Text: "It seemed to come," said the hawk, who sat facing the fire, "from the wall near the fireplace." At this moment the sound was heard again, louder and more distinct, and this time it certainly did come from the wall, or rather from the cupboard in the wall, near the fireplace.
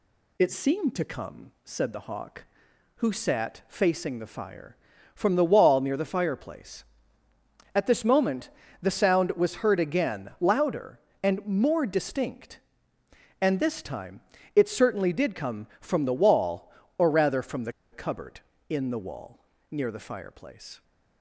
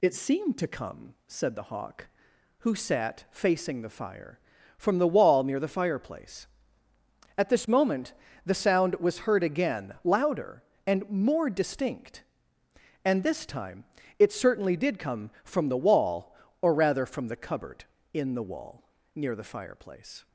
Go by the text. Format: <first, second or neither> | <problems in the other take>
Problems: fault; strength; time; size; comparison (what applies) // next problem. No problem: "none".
second | pauses between "moment" and "the"; slight; at 8.4 s; 0.32 s long; slight in the second // pauses between "time" and "it"; slight; at 14.2 s; 0.34 s long; slight in the second // pauses between "the" and "cupboard"; slight; at 17.7 s; 0.20 s long